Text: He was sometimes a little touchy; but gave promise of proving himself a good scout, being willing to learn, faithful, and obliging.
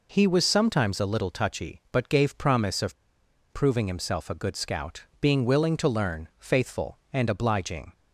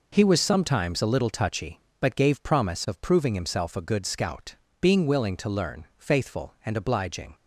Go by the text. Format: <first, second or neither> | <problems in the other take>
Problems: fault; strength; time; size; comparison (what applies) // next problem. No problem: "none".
second | pauses between "of" and "proving"; noticeable; at 2.9 s; 0.57 s long